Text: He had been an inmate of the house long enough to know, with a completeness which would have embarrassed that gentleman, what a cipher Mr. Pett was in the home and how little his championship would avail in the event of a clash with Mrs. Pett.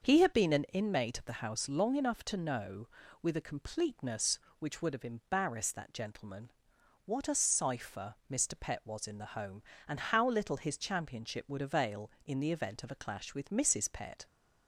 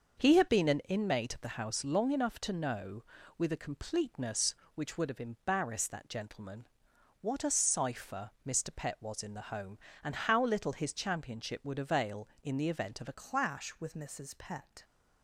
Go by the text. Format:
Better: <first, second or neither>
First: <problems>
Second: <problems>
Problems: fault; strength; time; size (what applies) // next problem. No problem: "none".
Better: first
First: starts louder than the rest; until 1.0 s; 6.5 dB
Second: starts louder than the rest; until 1.2 s; 6.5 dB // changes voice at "clash"; from 13.1 s on; 1.7 s long